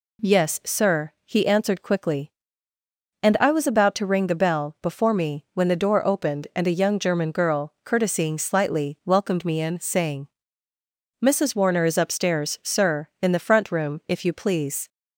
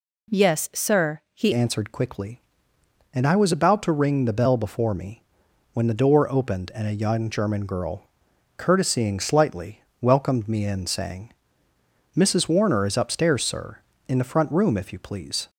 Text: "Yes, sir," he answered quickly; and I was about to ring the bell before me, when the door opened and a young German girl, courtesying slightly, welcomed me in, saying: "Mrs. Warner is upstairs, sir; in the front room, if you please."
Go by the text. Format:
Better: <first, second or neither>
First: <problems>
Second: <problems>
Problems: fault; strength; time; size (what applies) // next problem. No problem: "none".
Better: first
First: none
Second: changes voice at "answered"; from 1.5 s on; 13.9 s long